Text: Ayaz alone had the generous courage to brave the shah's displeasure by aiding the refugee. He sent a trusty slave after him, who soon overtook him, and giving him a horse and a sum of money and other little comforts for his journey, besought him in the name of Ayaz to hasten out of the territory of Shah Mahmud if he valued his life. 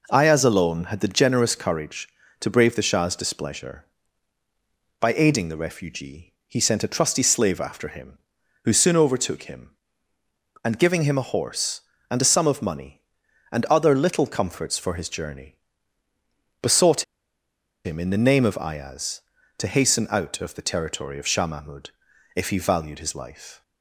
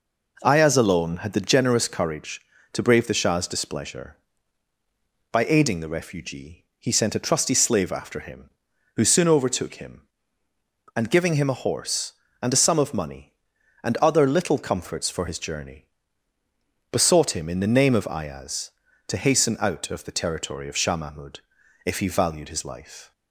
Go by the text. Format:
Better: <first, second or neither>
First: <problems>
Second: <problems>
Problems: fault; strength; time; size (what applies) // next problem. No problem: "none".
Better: second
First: pauses between "besought" and "him"; noticeable; at 17.0 s; 0.81 s long // pauses between "Mahmud" and "if"; noticeable; at 21.8 s; 0.46 s long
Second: pauses between "Mahmud" and "if"; noticeable; at 21.3 s; 0.46 s long